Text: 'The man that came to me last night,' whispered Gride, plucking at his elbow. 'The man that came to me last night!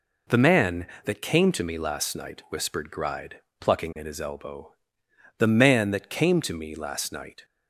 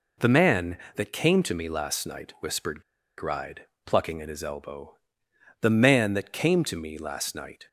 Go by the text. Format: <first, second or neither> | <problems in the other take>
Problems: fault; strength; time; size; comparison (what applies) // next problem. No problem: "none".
first | pauses between "whispered" and "Gride"; at 2.8 s; 0.36 s long